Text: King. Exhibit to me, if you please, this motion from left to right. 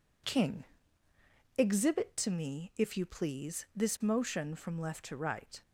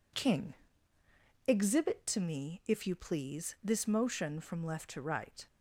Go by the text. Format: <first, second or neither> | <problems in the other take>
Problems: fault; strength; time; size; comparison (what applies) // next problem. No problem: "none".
neither | none